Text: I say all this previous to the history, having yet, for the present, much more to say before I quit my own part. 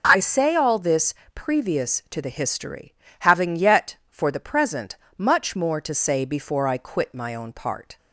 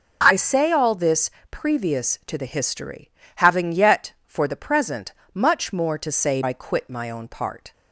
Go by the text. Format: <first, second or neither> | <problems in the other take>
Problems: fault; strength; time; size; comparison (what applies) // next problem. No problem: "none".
first | pauses between "this" and "previous"; slight; at 1.3 s; 0.18 s long; slight in the first // skips "before"; at 6.4 s